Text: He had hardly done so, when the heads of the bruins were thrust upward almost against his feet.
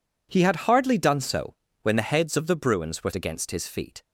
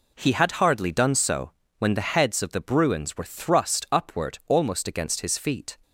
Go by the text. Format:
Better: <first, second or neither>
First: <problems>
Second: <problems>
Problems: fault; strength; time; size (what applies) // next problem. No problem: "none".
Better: second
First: skips "thrust upward almost"; at 3.1 s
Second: none